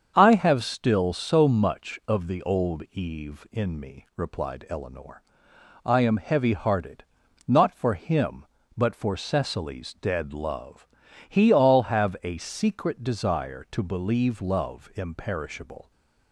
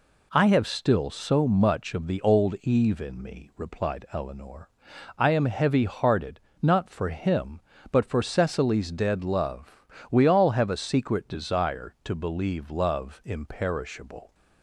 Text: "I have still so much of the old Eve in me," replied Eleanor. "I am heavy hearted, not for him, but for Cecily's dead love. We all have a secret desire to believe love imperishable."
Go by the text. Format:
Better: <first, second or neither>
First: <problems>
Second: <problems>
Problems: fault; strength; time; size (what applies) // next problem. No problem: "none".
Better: second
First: starts louder than the rest; strong; until 1.1 s; 7 dB // says "He" for "We"; at 11.2 s // stays silent after the last word; slight; from 15.8 s on; 0.5 s long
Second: none